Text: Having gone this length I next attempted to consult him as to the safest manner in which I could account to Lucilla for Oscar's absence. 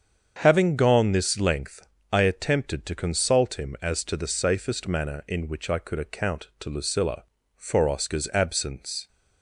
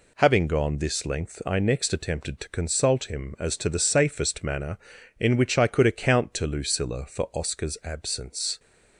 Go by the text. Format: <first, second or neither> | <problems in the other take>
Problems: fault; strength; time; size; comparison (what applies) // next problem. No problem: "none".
second | starts louder than the rest; strong; until 1.4 s; 7.5 dB // pauses between "length" and "I"; slight; at 1.8 s; 0.26 s long // skips "next"; at 2.2 s